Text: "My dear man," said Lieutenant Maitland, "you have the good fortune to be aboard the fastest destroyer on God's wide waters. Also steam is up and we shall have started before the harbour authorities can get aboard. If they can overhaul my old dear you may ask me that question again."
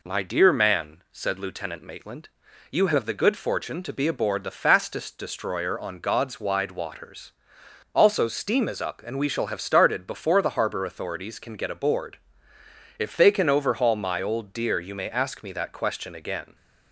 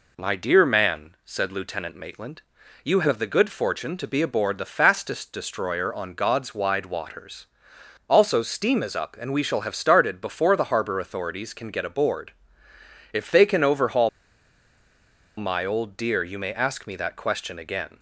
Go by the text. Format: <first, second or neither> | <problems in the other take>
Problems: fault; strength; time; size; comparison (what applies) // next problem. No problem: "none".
first | pauses between "overhaul" and "my"; strong; at 14.0 s; 1.2 s long